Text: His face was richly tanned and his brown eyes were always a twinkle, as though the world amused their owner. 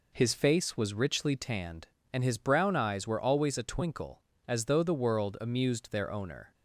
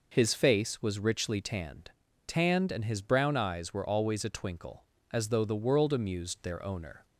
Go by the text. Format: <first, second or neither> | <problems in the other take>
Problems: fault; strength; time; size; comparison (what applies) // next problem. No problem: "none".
first | says "tanned" twice; at 2.2 s